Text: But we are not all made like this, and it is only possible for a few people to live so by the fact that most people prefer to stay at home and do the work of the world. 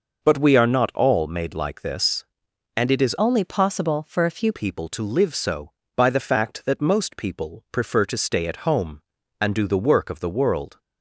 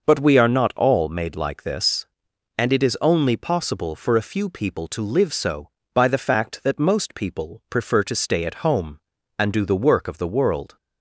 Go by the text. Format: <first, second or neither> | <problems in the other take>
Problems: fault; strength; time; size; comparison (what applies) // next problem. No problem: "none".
second | changes voice from "only" to "few"; from 3.1 to 4.5 s; 1.4 s long